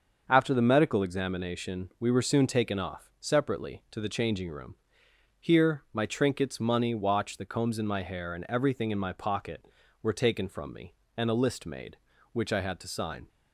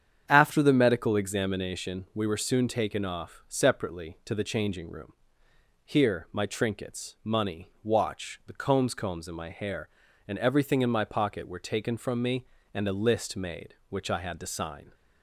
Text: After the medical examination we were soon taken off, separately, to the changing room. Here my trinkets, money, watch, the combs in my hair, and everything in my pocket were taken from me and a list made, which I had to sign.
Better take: first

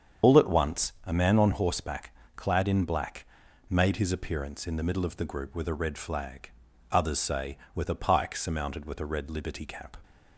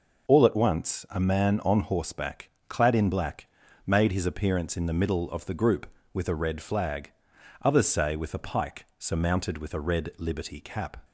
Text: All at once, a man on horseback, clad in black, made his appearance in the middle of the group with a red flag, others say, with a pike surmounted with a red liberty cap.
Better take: second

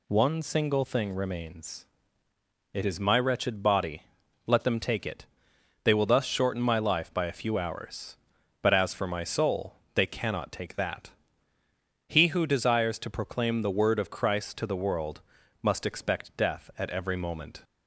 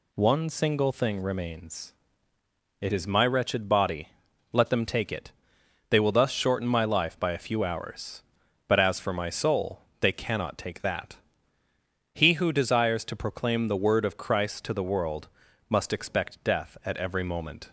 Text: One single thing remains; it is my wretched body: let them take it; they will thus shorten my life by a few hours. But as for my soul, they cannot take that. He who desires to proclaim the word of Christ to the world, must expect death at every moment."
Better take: neither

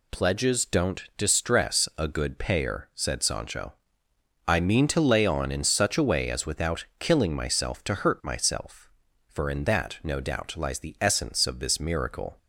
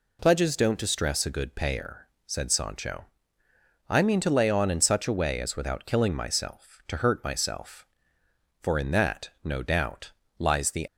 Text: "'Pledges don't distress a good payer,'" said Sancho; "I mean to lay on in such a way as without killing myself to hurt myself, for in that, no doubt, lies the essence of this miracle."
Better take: first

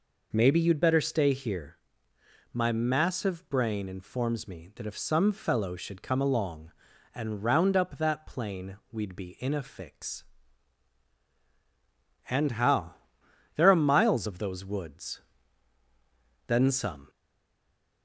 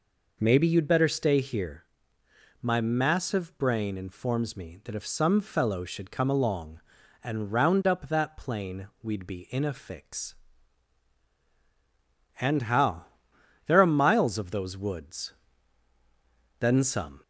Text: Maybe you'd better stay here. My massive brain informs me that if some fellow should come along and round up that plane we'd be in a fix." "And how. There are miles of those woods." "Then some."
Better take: second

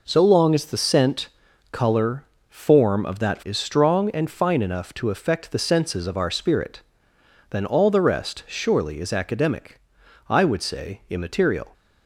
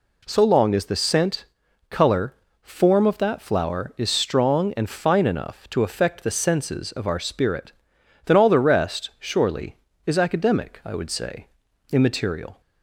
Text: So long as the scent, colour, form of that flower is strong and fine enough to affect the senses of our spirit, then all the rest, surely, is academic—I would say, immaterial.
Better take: second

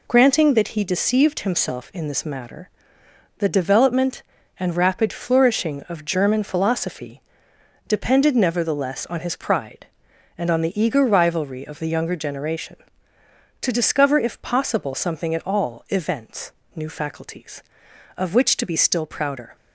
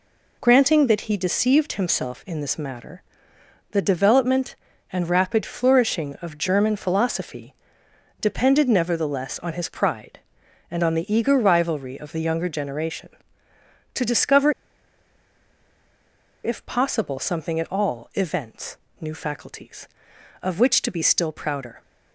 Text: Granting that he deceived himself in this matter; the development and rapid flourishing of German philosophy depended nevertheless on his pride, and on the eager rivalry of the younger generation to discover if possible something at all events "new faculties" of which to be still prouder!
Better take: first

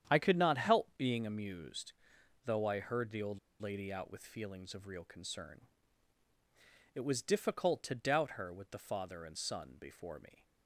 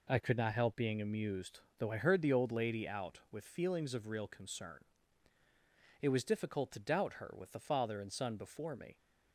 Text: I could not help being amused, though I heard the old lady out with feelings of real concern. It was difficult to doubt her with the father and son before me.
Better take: second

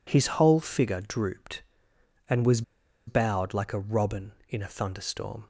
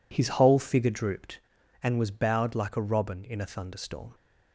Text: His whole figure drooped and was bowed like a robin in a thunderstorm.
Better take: second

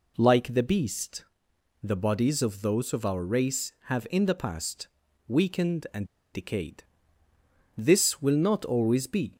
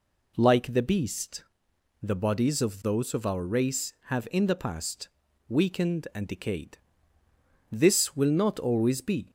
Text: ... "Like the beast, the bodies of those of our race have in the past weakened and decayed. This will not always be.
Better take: second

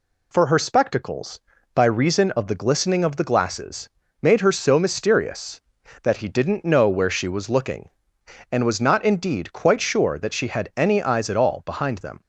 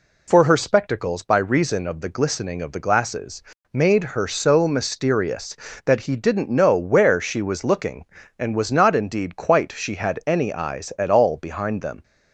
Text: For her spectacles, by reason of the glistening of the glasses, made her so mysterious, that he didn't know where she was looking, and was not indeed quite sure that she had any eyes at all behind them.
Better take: first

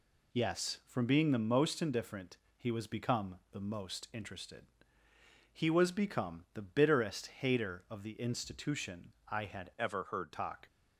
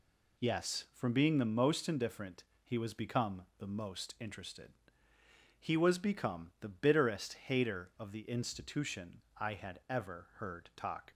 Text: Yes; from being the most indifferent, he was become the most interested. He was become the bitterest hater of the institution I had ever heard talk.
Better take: second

